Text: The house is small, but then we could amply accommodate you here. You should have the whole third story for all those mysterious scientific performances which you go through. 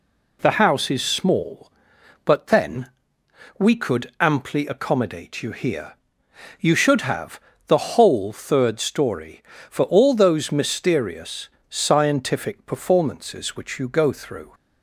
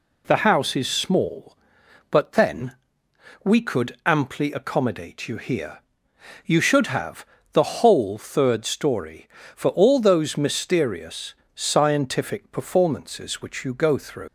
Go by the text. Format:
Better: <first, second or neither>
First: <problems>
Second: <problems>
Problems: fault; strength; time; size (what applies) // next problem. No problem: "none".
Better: first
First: pauses between "then" and "we"; noticeable; at 2.8 s; 0.68 s long // pauses between "have" and "the"; slight; at 7.3 s; 0.28 s long // pauses between "mysterious" and "scientific"; slight; at 11.4 s; 0.20 s long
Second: pauses between "then" and "we"; noticeable; at 2.7 s; 0.68 s long // pauses between "have" and "the"; slight; at 7.2 s; 0.28 s long // pauses between "mysterious" and "scientific"; slight; at 11.3 s; 0.20 s long // leaves "through" unfinished; at 14.2 s; 115 ms